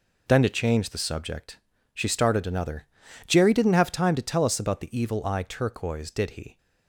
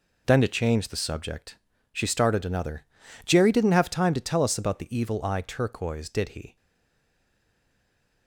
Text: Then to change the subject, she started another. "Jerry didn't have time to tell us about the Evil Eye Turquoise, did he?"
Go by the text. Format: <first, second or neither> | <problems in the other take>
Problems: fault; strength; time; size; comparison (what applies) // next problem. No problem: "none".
first | stays silent after the last word; noticeable; from 6.5 s on; 1.7 s long